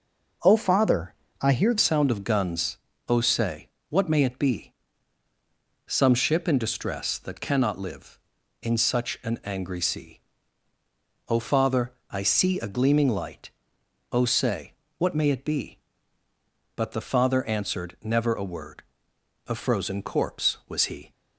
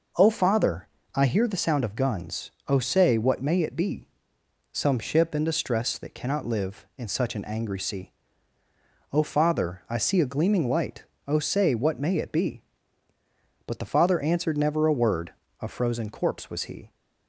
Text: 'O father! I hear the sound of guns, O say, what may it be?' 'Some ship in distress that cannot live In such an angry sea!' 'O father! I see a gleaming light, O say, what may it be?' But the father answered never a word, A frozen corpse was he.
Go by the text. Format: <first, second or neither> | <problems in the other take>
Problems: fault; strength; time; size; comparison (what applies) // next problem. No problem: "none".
second | changes voice at "sound"; from 1.7 s on; 19.4 s long